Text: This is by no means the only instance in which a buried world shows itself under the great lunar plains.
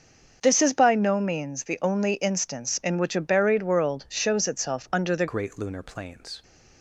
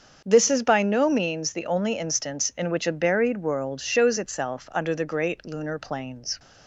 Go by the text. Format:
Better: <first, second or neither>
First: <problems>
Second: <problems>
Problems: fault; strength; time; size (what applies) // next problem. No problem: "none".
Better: second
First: starts louder than the rest; until 1.4 s; 6.5 dB // changes voice at "great"; from 5.2 s on; 1.2 s long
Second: starts louder than the rest; until 1.2 s; 7 dB